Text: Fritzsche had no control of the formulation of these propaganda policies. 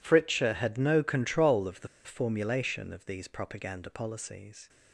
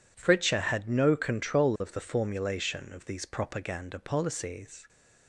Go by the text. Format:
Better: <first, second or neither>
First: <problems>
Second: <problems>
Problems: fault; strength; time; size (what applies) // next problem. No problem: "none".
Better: second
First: pauses between "the" and "formulation"; slight; at 1.8 s; 0.17 s long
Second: none